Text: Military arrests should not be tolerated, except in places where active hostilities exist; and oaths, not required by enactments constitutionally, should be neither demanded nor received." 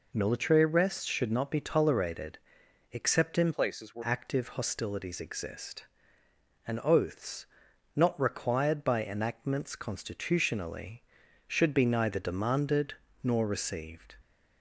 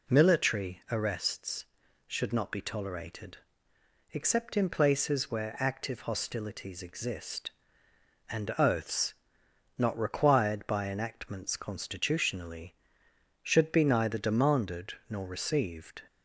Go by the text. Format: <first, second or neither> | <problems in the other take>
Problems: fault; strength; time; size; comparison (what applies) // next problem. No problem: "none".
second | changes voice from "places" to "where"; from 3.5 to 4.0 s; 0.5 s long // pauses between "demanded" and "nor"; slight; at 12.9 s; 0.30 s long; slight in the second